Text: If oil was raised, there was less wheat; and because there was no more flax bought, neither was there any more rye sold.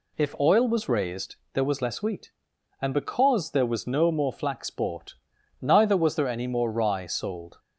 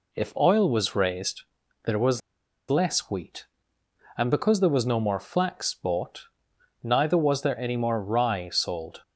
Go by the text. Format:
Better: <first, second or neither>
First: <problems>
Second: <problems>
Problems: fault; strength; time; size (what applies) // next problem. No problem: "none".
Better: first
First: none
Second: pauses between "was" and "less"; noticeable; at 2.2 s; 0.49 s long